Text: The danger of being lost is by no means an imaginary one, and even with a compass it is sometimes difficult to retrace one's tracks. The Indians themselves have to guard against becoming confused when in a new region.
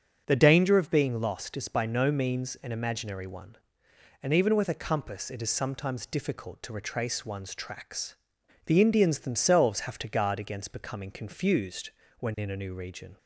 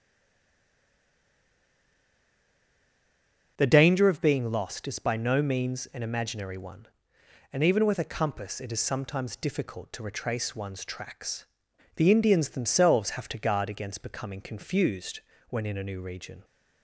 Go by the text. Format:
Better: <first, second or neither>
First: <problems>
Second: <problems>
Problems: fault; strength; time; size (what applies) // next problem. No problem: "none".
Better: first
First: starts louder than the rest; strong; until 1.2 s; 7 dB // pauses between "confused" and "when"; slight; at 11.9 s; 0.30 s long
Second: stays silent before the first word; strong; until 3.5 s; 3.5 s long // starts louder than the rest; strong; until 4.5 s; 7 dB // pauses between "confused" and "when"; slight; at 15.2 s; 0.30 s long